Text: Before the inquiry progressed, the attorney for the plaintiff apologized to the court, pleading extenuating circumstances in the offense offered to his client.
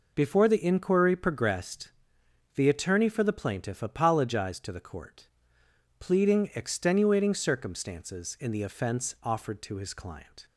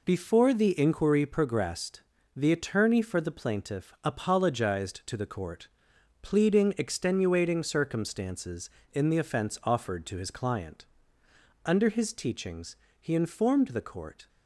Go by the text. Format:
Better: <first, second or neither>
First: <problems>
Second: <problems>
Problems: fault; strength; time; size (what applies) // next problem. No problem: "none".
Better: first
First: none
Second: goes on to say "Under his teachings he informed the court"; strong; from 11.6 s on; 2.6 s long